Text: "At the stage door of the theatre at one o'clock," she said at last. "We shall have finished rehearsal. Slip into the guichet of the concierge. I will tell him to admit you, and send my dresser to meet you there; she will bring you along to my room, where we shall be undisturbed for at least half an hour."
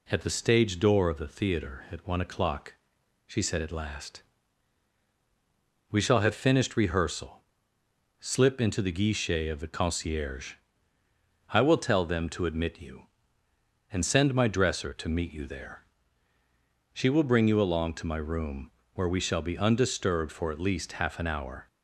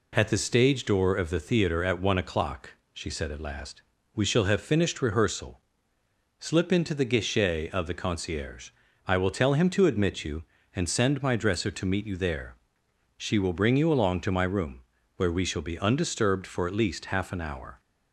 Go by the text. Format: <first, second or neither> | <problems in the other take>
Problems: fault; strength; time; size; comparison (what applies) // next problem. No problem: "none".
second | says "them" for "him"; at 12.0 s